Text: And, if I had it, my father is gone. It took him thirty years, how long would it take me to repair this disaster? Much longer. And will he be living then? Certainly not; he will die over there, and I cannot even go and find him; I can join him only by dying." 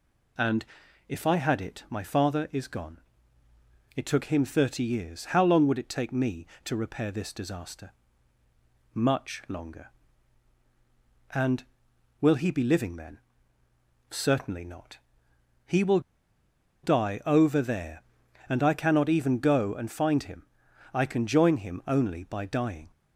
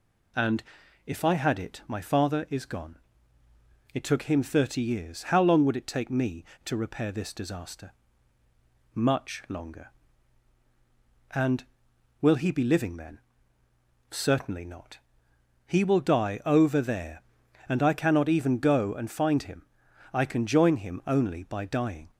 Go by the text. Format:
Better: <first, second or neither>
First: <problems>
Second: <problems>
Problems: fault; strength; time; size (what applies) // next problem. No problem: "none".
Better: second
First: pauses between "will" and "die"; noticeable; at 15.9 s; 0.83 s long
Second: none